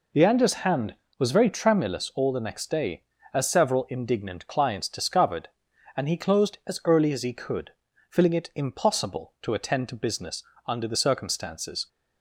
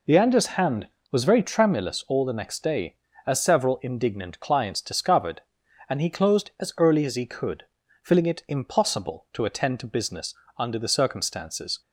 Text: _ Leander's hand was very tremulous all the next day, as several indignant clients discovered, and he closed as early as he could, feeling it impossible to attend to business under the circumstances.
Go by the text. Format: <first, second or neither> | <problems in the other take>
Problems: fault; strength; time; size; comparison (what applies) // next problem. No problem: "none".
neither | pauses between "business" and "under"; slight; the same in both